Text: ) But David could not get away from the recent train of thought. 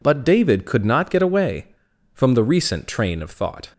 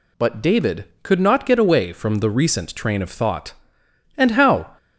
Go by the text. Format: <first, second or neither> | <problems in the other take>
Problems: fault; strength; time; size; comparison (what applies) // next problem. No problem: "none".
first | goes on to say "And how"; from 4.1 s on; 0.60 s long